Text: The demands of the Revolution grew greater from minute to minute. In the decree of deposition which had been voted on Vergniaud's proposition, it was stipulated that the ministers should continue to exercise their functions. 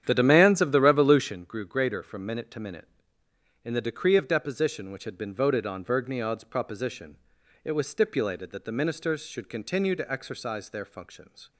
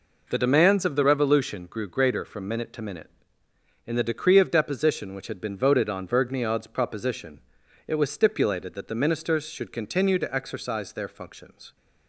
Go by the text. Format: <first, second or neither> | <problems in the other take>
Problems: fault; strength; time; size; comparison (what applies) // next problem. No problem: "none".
second | starts louder than the rest; strong; until 1.3 s; 9.5 dB